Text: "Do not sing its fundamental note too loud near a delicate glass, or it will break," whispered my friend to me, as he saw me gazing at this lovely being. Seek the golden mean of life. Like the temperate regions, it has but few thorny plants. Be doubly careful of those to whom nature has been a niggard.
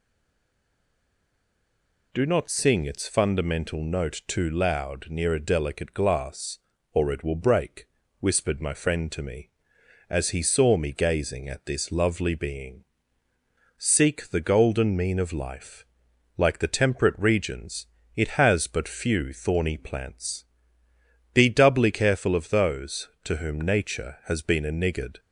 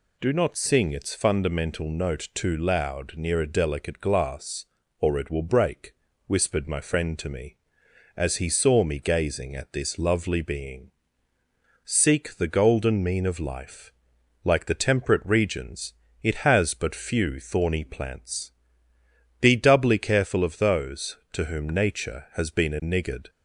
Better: second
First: stays silent before the first word; until 2.1 s; 2.1 s long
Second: none

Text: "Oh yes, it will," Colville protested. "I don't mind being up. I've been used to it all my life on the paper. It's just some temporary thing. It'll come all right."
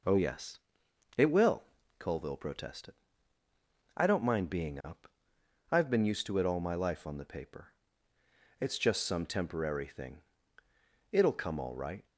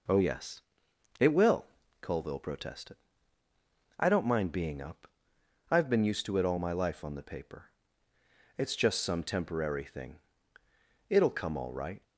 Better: neither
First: none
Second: none

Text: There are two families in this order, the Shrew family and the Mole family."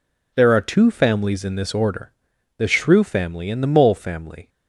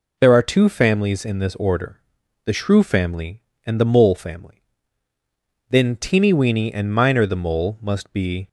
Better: first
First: none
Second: goes on to say "Then Teeny Weeny and Miner the Mole must be"; strong; from 5.6 s on; 2.8 s long

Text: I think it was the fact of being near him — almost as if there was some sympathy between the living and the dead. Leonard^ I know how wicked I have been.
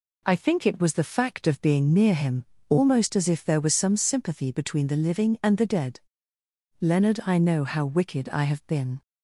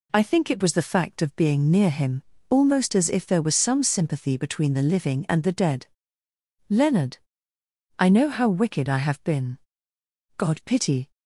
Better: first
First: none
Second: pauses between "Leonard" and "I"; noticeable; at 7.1 s; 0.80 s long // goes on to say "God pity"; noticeable; from 10.3 s on; 0.72 s long

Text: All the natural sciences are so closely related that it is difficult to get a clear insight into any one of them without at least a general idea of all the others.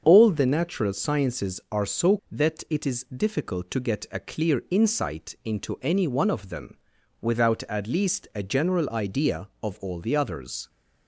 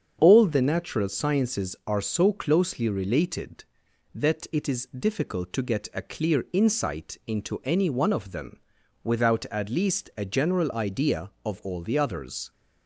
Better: second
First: starts louder than the rest; until 1.0 s; 7 dB // skips "closely related"; at 2.2 s // pauses between "them" and "without"; noticeable; at 6.7 s; 0.46 s long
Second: starts louder than the rest; strong; until 1.2 s; 7.5 dB // pauses between "them" and "without"; noticeable; at 8.5 s; 0.46 s long

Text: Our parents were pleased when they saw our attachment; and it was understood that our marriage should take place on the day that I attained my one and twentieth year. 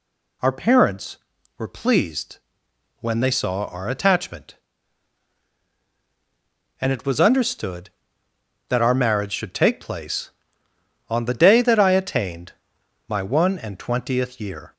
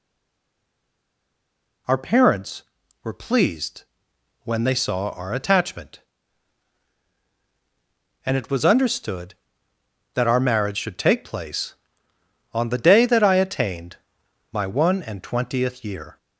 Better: first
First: pauses between "pleased" and "when"; noticeable; at 2.3 s; 0.60 s long // pauses between "attained" and "my"; noticeable; at 12.5 s; 0.56 s long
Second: stays silent before the first word; noticeable; until 1.8 s; 1.8 s long // pauses between "pleased" and "when"; noticeable; at 3.8 s; 0.58 s long // pauses between "attained" and "my"; noticeable; at 13.9 s; 0.56 s long

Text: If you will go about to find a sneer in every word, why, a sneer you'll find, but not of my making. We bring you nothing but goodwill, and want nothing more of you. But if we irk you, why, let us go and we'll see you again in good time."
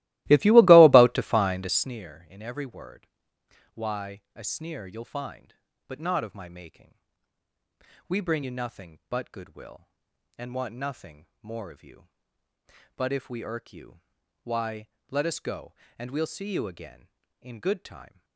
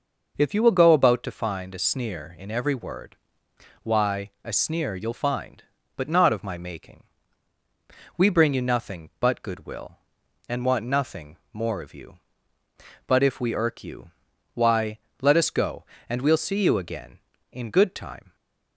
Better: second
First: starts louder than the rest; strong; until 2.0 s; 17.5 dB // pauses between "nothing" and "more"; slight; at 11.2 s; 0.16 s long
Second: pauses between "nothing" and "more"; slight; at 11.3 s; 0.16 s long

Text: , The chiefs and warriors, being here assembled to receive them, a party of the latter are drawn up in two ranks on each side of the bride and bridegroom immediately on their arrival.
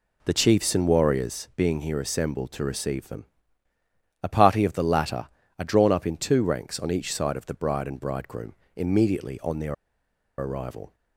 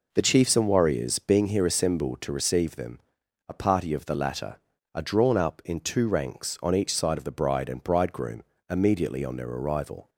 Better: second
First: pauses between "bridegroom" and "immediately"; slight; at 8.5 s; 0.22 s long // pauses between "their" and "arrival"; noticeable; at 9.7 s; 0.63 s long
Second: pauses between "bridegroom" and "immediately"; slight; at 8.4 s; 0.30 s long

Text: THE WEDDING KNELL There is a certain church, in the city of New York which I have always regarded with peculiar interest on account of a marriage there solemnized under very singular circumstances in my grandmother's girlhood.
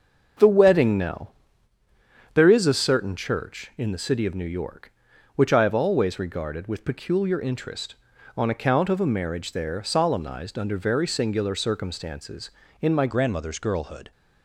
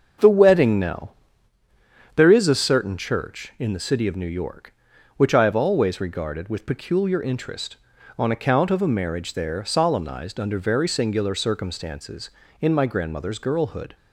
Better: second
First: starts louder than the rest; until 2.4 s; 6.5 dB // pauses between "KNELL" and "There"; at 1.3 s; 1.0 s long // changes voice at "grandmother's"; from 13.0 s on; 1.1 s long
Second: starts louder than the rest; until 2.2 s; 6.5 dB // pauses between "KNELL" and "There"; at 1.1 s; 1.0 s long

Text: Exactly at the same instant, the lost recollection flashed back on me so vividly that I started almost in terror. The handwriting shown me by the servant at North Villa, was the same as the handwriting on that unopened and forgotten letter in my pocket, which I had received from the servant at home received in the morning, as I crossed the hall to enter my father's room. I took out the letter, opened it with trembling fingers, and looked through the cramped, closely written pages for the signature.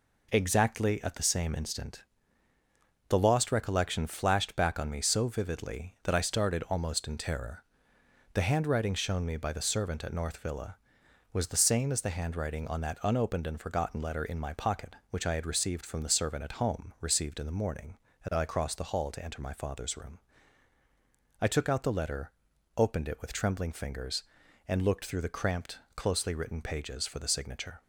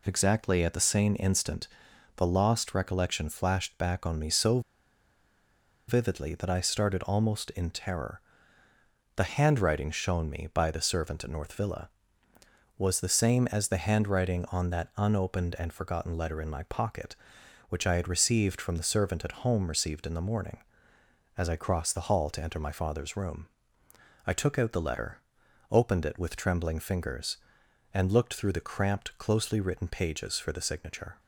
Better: first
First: none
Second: pauses between "so" and "vividly"; strong; at 4.5 s; 1.2 s long

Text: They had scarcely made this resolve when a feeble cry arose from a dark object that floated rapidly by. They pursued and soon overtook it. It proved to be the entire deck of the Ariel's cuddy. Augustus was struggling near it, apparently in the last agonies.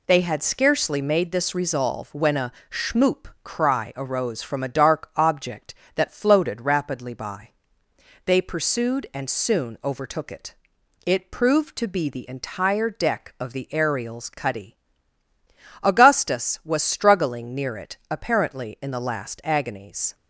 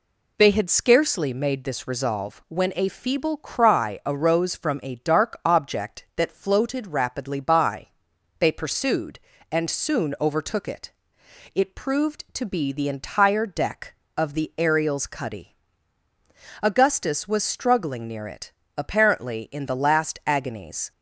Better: second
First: says "schmoop" for "feeble"; at 2.6 s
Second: none

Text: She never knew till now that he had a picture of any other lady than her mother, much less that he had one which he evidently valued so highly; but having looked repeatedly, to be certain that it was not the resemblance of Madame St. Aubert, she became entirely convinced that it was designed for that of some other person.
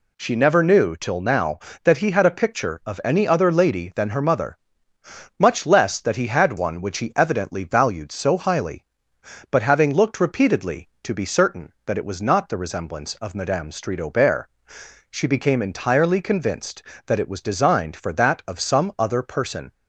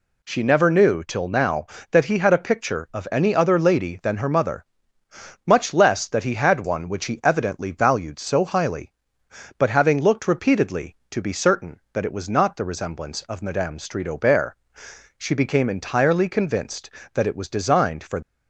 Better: first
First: none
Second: stops before "that of some other person"; at 18.2 s

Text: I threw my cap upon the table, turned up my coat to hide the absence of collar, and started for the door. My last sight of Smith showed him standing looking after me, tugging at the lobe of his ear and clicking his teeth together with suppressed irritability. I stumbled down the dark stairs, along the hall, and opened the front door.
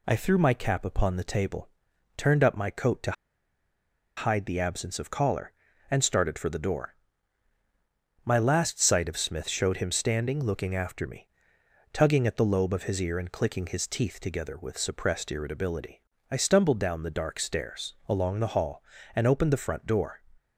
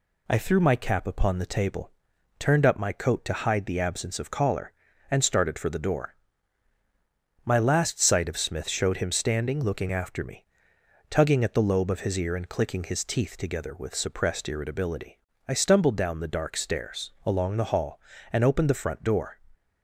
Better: second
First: pauses between "to" and "hide"; at 3.1 s; 1.0 s long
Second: none

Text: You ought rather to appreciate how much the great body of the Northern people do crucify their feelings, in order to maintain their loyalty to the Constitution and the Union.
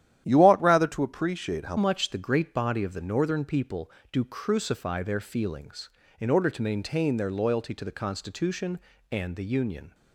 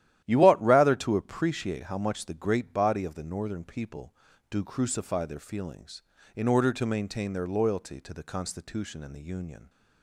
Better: second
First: starts louder than the rest; strong; until 1.2 s; 11 dB // changes voice at "much"; from 1.7 s on; 8.2 s long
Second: starts louder than the rest; strong; until 1.2 s; 12 dB

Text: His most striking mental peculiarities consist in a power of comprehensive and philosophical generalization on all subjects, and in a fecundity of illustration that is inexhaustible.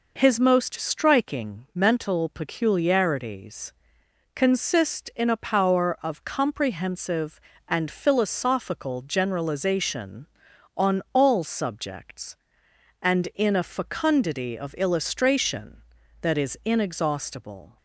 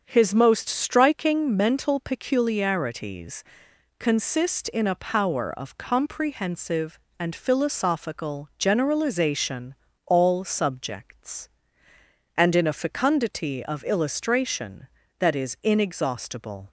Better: first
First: pauses between "peculiarities" and "consist"; noticeable; at 3.7 s; 0.58 s long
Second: starts louder than the rest; until 1.0 s; 7 dB // pauses between "peculiarities" and "consist"; noticeable; at 3.4 s; 0.54 s long // skips "on"; at 9.8 s

